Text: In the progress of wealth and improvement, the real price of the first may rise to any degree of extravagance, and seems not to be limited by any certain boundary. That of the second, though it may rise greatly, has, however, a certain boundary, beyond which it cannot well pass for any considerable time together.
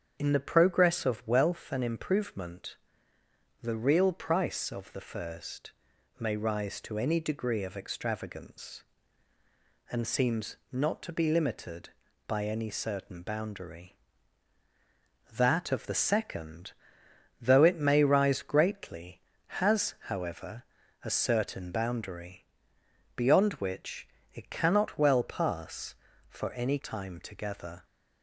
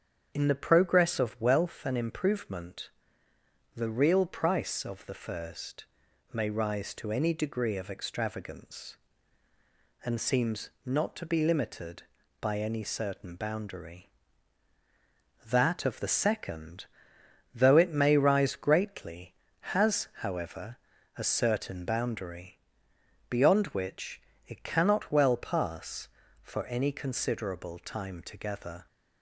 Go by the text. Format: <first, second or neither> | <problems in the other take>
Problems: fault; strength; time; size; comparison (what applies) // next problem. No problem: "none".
second | starts louder than the rest; strong; until 1.2 s; 8 dB; strong in the second // pauses between "first" and "may"; noticeable; at 5.7 s; 0.48 s long; noticeable in the second // pauses between "seems" and "not"; slight; at 10.5 s; 0.16 s long; slight in the second // pauses between "which" and "it"; slight; at 24.0 s; 0.24 s long; slight in the second // skips "considerable"; at 26.7 s